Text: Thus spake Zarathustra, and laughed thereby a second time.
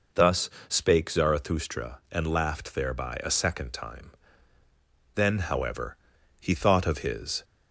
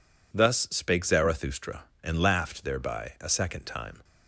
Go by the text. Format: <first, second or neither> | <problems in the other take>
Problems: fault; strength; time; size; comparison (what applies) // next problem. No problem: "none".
second | pauses between "Thus" and "spake"; slight; at 0.5 s; 0.18 s long // goes on to say "Then however he thought of his"; strong; from 5.1 s on; 2.2 s long